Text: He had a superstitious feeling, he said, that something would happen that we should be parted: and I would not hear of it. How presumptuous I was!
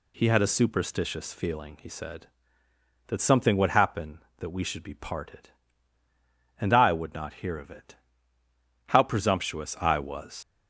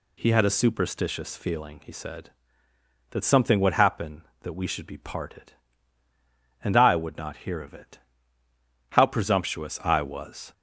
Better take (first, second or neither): second